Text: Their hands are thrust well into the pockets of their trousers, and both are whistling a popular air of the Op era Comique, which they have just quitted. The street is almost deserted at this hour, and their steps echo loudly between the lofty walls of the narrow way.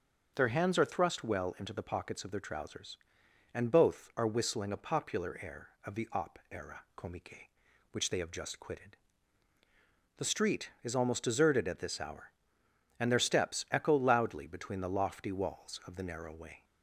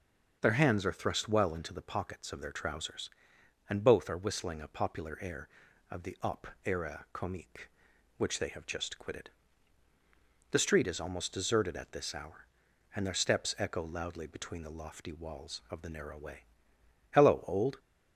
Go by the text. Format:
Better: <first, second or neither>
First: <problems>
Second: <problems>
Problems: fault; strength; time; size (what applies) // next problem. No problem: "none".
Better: first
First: starts louder than the rest; until 1.3 s; 6.5 dB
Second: starts louder than the rest; until 1.4 s; 6.5 dB // pauses between "Op" and "era"; slight; at 6.4 s; 0.18 s long // goes on to say "Hello old"; noticeable; from 17.1 s on; 0.66 s long